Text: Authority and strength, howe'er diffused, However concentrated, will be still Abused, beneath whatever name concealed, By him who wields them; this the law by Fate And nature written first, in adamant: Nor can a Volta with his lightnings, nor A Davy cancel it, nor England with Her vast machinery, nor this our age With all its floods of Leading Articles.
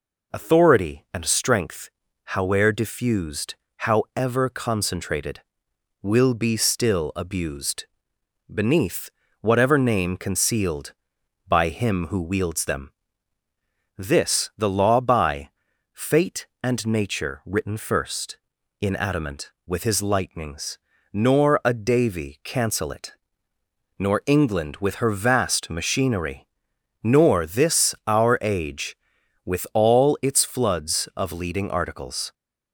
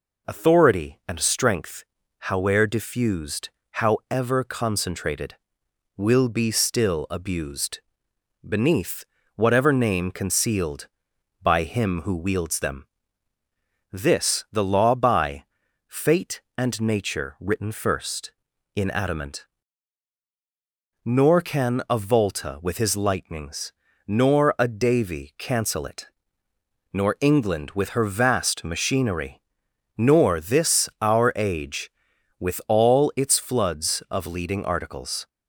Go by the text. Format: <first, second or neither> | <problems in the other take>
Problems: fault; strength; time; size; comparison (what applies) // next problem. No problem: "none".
second | pauses between "beneath" and "whatever"; slight; at 9.1 s; 0.30 s long; slight in the second // pauses between "by" and "Fate"; at 15.4 s; 0.44 s long; also in the second // skips "Nor can a Volta"; at 19.5 s